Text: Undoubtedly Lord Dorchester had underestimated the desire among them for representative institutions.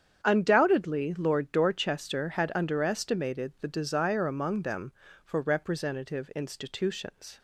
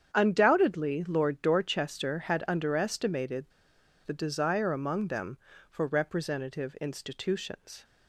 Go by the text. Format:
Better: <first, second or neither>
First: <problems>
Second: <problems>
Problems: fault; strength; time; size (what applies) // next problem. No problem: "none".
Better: first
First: starts louder than the rest; strong; until 1.2 s; 8 dB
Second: starts louder than the rest; strong; until 1.1 s; 8 dB // pauses between "underestimated" and "the"; noticeable; at 3.4 s; 0.60 s long